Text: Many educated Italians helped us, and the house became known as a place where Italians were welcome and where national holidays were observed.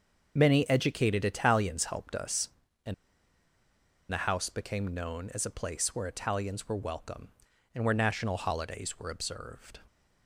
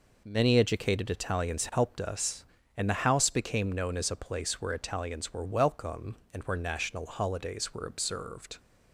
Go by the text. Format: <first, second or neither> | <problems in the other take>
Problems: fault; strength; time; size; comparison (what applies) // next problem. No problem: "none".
second | starts louder than the rest; noticeable; until 1.3 s; 6 dB // pauses between "and" and "the"; at 2.9 s; 1.1 s long